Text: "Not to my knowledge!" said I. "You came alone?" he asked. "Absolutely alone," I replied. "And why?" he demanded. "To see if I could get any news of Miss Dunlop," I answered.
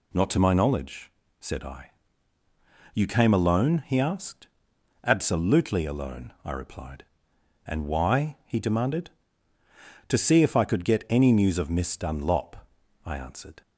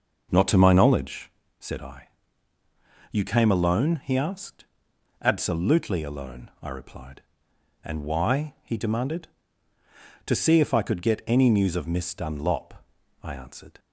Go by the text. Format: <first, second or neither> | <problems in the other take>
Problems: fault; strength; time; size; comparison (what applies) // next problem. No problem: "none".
first | starts louder than the rest; noticeable; until 1.5 s; 5.5 dB